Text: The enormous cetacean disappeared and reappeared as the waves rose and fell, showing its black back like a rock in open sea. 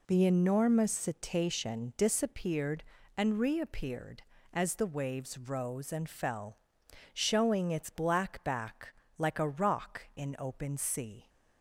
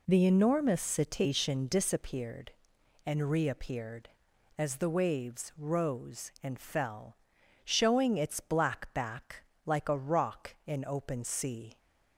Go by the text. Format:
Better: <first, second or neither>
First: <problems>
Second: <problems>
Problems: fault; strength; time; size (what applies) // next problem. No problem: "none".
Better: neither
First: pauses between "back" and "like"; slight; at 8.9 s; 0.24 s long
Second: pauses between "back" and "like"; slight; at 9.4 s; 0.24 s long